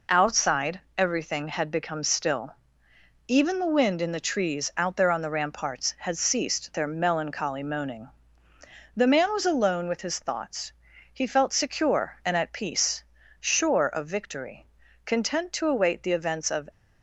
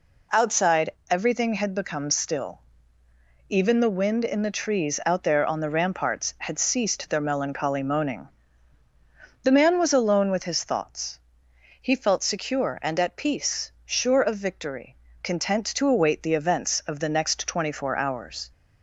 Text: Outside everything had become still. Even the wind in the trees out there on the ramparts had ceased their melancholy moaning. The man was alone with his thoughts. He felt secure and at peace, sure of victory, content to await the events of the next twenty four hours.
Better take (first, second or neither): second